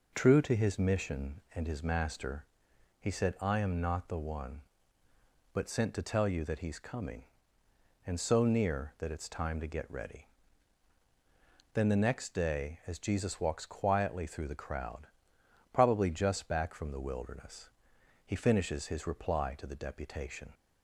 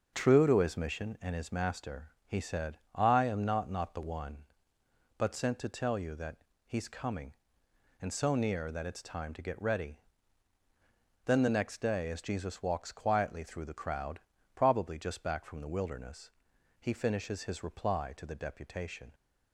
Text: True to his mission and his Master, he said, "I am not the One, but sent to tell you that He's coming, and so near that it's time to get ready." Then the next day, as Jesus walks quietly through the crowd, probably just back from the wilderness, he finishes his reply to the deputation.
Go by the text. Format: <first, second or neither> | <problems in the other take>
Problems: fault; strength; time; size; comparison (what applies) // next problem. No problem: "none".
first | starts louder than the rest; until 1.1 s; 6.5 dB // says "not" twice; at 3.7 s // pauses between "that" and "He's"; slight; at 6.3 s; 0.30 s long